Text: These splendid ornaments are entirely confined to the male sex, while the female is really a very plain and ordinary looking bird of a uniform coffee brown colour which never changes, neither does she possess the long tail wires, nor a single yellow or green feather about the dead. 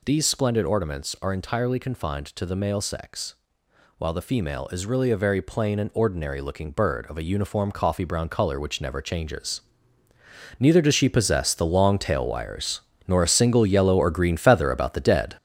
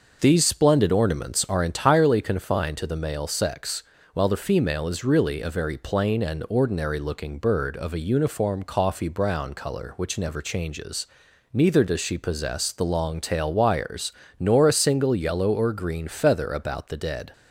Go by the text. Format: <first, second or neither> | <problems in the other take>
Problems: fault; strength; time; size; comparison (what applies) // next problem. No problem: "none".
second | gets louder; noticeable; throughout; 6 dB